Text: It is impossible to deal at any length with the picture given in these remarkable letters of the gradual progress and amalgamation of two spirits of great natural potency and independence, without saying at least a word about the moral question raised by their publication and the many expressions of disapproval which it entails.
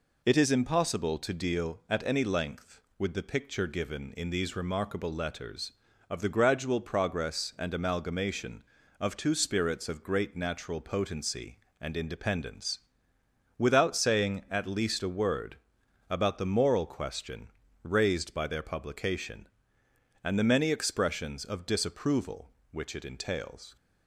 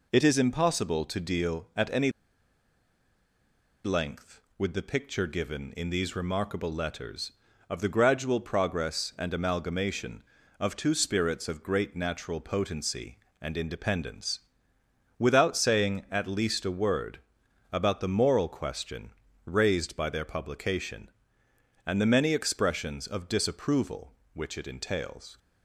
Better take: first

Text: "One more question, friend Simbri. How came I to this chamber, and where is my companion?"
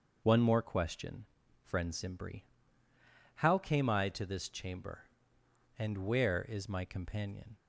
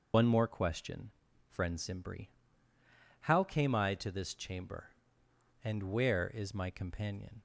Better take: first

